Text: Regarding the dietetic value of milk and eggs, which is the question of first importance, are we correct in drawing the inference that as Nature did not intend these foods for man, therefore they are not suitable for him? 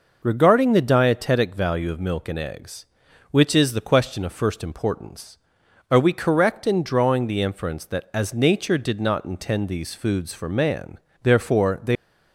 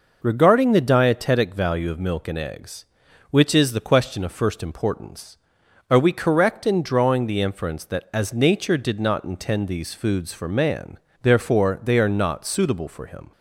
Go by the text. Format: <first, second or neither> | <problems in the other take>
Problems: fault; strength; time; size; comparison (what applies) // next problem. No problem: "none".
second | stops before "are not suitable for him"; at 11.9 s